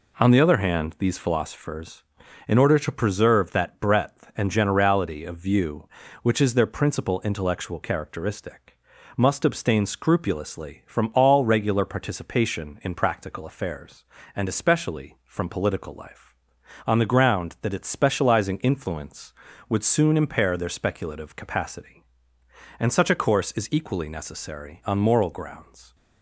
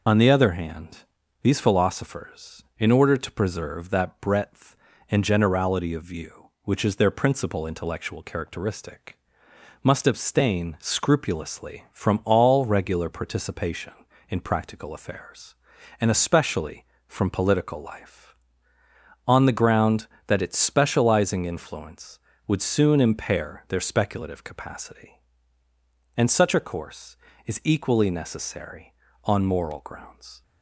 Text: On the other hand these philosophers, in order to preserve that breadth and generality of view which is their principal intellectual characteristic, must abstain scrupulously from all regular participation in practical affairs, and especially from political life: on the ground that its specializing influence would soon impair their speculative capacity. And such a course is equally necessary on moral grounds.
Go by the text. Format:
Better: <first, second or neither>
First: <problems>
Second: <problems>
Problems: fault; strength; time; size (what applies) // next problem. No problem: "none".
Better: first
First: none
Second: loses the start of "On"; at 0.0 s; 40 ms // pauses between "hand" and "these"; at 0.9 s; 0.44 s long